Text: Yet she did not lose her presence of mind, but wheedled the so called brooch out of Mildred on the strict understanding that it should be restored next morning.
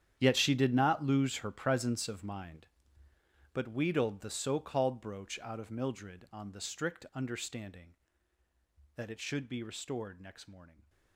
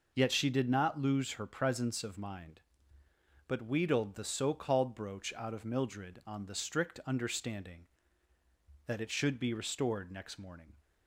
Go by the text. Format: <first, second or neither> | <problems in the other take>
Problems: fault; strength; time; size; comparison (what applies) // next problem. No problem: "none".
second | gets quieter; strong; throughout; 17 dB